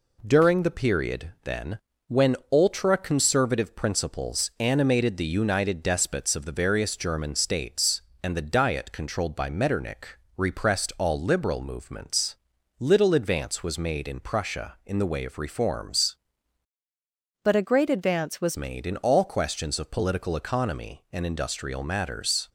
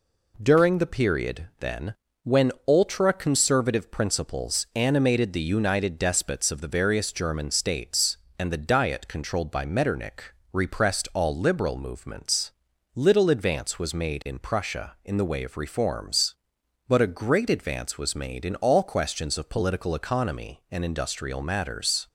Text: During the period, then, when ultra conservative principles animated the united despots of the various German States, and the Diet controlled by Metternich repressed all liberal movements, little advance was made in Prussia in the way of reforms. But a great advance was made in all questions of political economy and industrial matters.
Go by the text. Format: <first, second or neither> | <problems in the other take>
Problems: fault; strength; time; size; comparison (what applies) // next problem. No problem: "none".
second | pauses between "when" and "ultra"; slight; at 2.3 s; 0.16 s long; slight in the second // pauses between "Metternich" and "repressed"; slight; at 10.1 s; 0.18 s long; slight in the second // changes voice from "But" to "was"; from 17.4 to 18.5 s; 1.1 s long